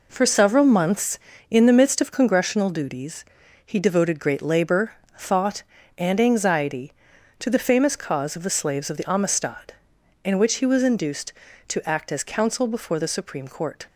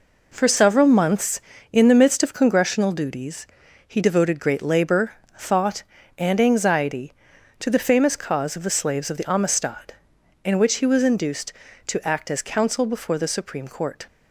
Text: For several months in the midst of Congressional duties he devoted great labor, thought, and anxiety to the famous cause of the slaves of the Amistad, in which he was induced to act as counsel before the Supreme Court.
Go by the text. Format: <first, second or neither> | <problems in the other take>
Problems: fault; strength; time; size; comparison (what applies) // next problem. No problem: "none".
neither | pauses between "duties" and "he"; the same in both